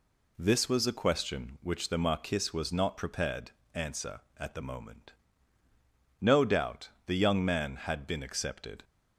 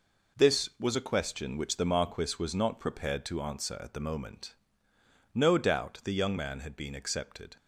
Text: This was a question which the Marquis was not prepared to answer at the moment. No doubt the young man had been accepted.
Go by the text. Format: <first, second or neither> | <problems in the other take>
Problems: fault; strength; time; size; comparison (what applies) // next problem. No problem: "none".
second | skips "to"; at 3.6 s // pauses between "doubt" and "the"; slight; at 6.8 s; 0.18 s long